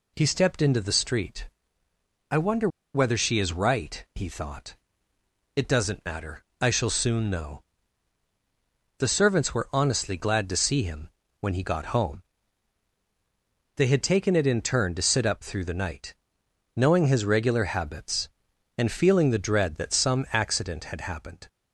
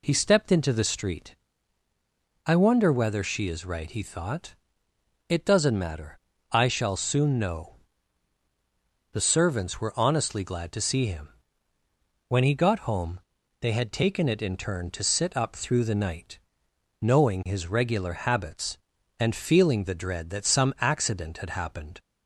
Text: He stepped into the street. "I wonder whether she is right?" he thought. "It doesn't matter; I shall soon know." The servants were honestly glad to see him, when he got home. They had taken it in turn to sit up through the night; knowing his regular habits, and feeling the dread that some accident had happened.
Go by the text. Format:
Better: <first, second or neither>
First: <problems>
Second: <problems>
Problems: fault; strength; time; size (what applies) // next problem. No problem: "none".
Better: second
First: pauses between "wonder" and "whether"; slight; at 2.6 s; 0.26 s long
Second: none